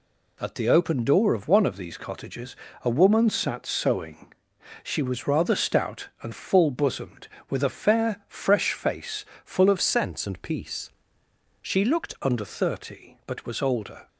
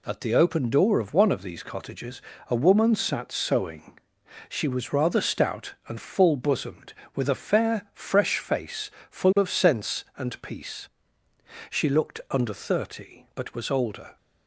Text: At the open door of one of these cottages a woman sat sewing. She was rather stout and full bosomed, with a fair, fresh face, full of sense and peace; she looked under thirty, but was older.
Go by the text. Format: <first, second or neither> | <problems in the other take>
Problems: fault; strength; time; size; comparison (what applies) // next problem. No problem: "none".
second | pauses between "cottages" and "a"; slight; at 2.5 s; 0.26 s long; slight in the second // changes voice from "sense" to "looked"; from 9.7 to 12.1 s; 2.4 s long